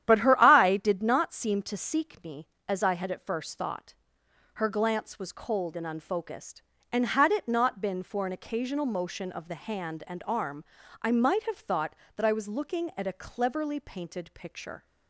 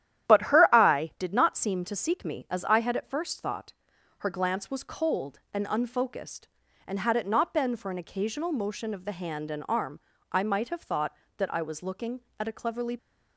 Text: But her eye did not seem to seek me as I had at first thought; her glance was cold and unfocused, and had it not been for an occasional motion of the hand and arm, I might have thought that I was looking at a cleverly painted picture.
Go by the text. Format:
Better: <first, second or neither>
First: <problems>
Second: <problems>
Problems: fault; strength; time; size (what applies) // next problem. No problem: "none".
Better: first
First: starts louder than the rest; strong; until 1.0 s; 10.5 dB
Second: starts louder than the rest; strong; until 1.3 s; 11 dB // stops before "painted picture"; at 12.9 s